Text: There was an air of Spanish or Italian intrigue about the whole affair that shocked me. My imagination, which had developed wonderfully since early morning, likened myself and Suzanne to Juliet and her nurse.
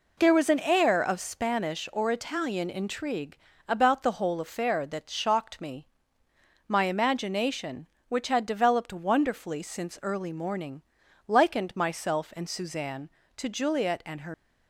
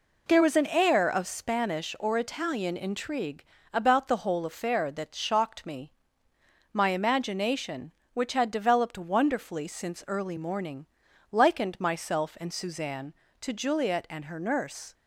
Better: second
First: pauses between "intrigue" and "about"; slight; at 3.3 s; 0.31 s long // stops before "nurse"; at 14.3 s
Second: pauses between "intrigue" and "about"; slight; at 3.4 s; 0.30 s long

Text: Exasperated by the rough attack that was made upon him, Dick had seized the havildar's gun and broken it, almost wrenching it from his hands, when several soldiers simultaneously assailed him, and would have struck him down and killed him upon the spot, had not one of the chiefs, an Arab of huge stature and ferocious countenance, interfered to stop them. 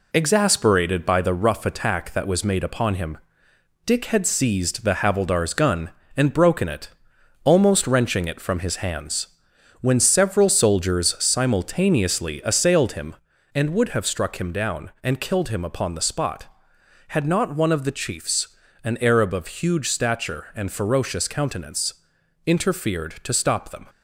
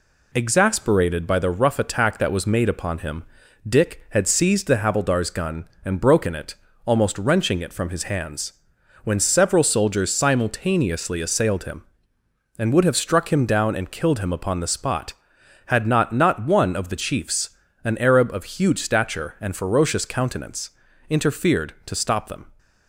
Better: first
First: none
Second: says "not" twice; at 16.1 s

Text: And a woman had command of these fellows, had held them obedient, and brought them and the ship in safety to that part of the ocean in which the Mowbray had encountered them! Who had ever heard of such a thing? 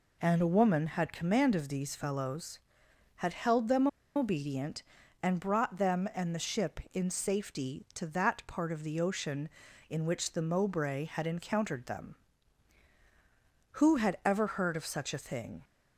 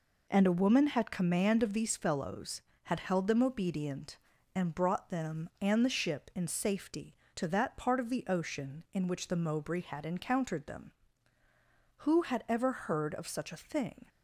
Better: second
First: pauses between "them" and "obedient"; slight; at 3.8 s; 0.29 s long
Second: none

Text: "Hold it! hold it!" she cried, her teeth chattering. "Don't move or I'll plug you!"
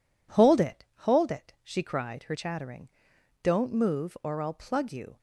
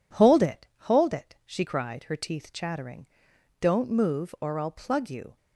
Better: second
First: skips "teeth"; at 2.3 s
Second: none

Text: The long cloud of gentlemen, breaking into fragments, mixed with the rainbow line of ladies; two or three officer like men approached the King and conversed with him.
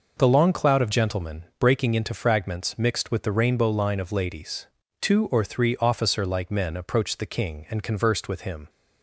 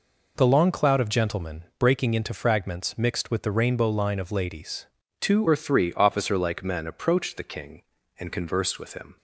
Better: first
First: none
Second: changes voice at "or"; from 5.4 s on; 3.7 s long

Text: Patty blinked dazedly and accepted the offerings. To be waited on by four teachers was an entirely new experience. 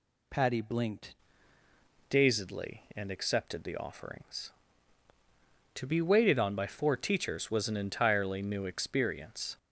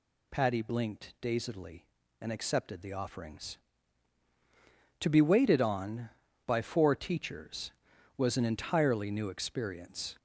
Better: second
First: changes voice at "dazedly"; from 2.1 s on; 7.4 s long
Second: none

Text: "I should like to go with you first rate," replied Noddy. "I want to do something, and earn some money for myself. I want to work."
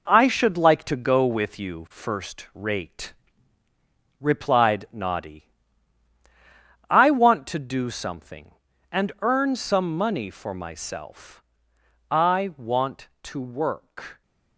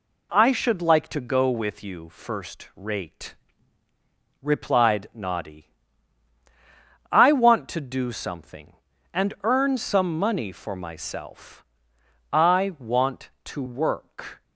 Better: second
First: gets quieter; strong; throughout; 8 dB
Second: none

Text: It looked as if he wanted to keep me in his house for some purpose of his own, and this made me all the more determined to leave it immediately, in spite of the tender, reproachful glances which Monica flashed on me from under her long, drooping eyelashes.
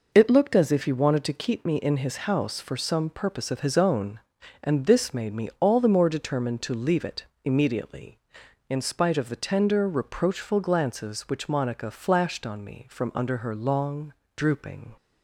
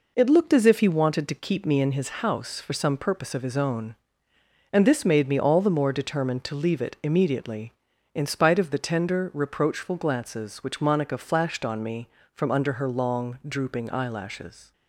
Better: second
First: pauses between "it" and "immediately"; slight; at 7.2 s; 0.22 s long // stops before "eyelashes"; at 14.9 s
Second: none

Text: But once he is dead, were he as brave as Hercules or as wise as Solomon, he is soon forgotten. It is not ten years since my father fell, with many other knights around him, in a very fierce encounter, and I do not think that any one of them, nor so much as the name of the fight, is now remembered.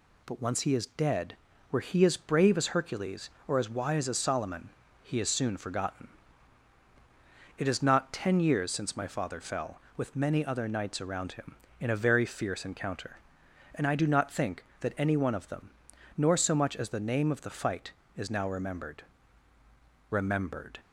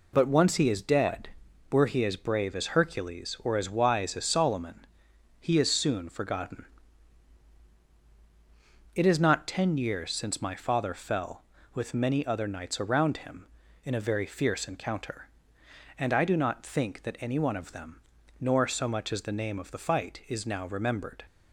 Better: second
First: says "remembered" twice; at 20.0 s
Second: none

